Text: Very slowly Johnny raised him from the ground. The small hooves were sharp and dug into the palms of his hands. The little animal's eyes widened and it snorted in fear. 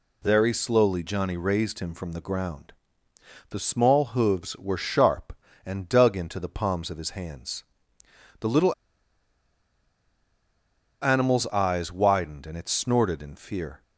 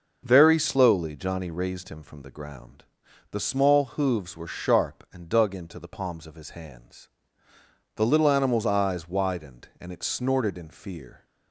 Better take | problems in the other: second | pauses between "little" and "animal's"; strong; at 8.7 s; 2.2 s long

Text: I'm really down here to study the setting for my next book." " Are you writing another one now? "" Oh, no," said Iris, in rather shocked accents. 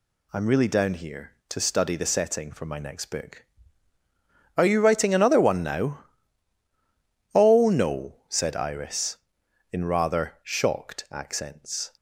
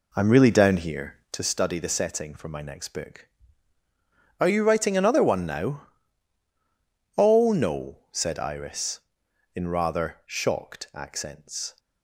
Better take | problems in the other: first | starts louder than the rest; slight; until 1.5 s; 3.5 dB

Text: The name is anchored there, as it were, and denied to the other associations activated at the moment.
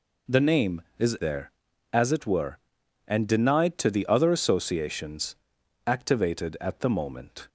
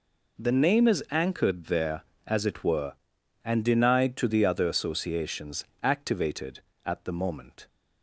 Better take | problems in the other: second | skips "anchored"; at 1.1 s // pauses between "associations" and "activated"; noticeable; at 5.3 s; 0.52 s long; slight in the second

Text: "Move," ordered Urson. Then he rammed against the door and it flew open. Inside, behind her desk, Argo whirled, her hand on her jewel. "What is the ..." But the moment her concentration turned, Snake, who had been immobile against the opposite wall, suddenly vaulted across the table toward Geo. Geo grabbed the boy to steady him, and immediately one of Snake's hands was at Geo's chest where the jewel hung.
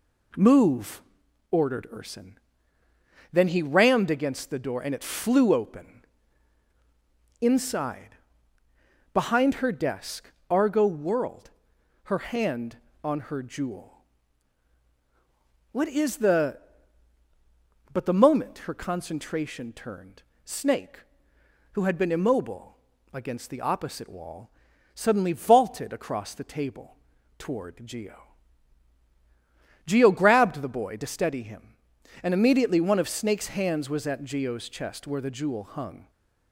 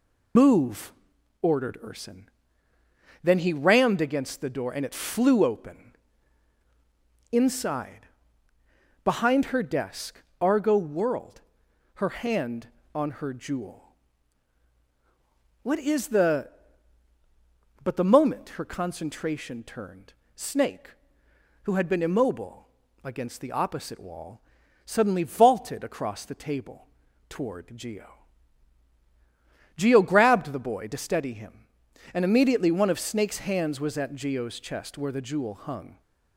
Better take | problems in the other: first | loses the start of "Move"; at 0.3 s; 115 ms // pauses between "immobile" and "against"; slight; at 22.6 s; 0.34 s long; slight in the first // pauses between "table" and "toward"; at 26.8 s; 0.42 s long; also in the first

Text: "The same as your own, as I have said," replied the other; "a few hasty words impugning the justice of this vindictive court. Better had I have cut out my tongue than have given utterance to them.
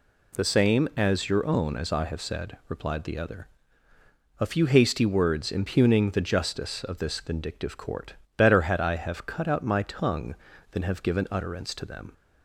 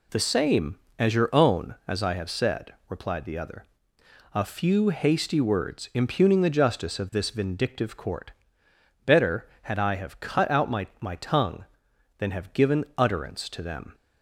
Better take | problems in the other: first | says "my" twice; at 10.9 s

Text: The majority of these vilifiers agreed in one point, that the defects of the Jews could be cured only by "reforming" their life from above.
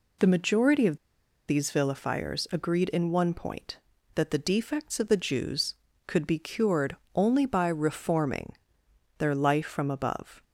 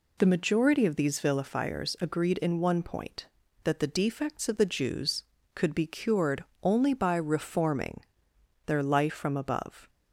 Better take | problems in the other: second | pauses between "of" and "these"; noticeable; at 0.9 s; 0.51 s long // pauses between "cured" and "only"; slight; at 6.9 s; 0.20 s long; slight in the second // pauses between "reforming" and "their"; noticeable; at 8.5 s; 0.64 s long; noticeable in the second

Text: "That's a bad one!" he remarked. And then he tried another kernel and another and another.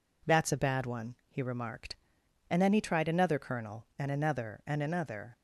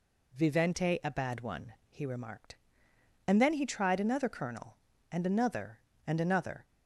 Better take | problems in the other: first | says "Vivente" for "That's"; at 0.3 s

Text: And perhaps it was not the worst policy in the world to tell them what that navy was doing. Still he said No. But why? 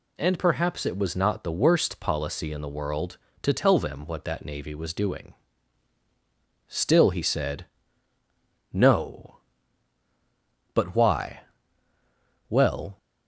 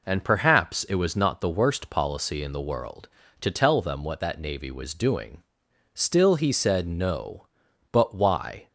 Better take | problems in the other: second | pauses between "said" and "No"; at 7.6 s; 1.0 s long // goes on to say "Well"; slight; from 12.4 s on; 0.48 s long

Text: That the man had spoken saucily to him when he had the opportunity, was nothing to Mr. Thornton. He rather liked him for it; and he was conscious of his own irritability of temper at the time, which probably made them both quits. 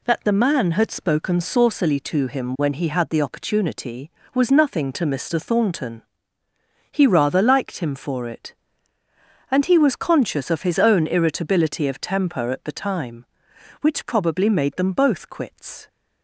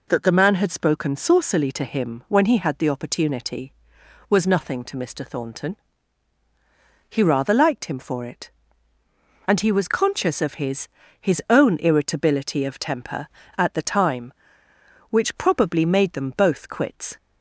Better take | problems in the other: first | says "his" twice; at 11.2 s

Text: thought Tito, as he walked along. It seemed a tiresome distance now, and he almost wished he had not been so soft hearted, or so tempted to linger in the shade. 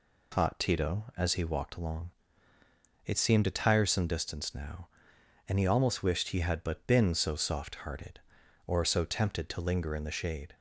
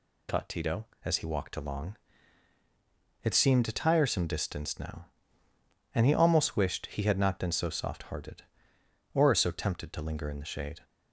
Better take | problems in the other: second | says "but" for "not"; at 6.6 s

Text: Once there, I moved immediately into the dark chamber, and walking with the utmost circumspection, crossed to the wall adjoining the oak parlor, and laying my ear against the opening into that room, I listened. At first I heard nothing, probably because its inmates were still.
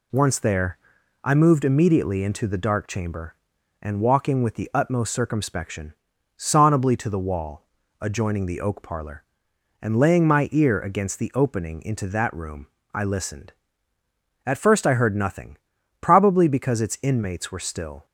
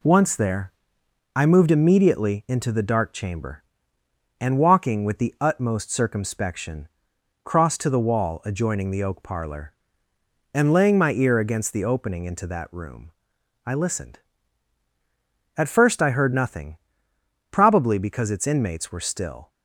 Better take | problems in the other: second | says "sonably" for "crossed"; at 6.3 s // pauses between "wall" and "adjoining"; at 7.6 s; 0.38 s long

